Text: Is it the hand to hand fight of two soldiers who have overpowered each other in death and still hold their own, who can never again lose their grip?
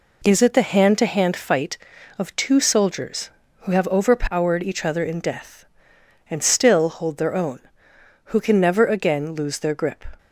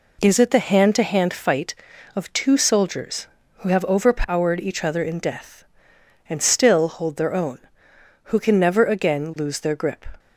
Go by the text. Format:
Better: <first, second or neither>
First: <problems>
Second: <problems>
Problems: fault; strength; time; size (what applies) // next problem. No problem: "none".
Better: neither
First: none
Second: none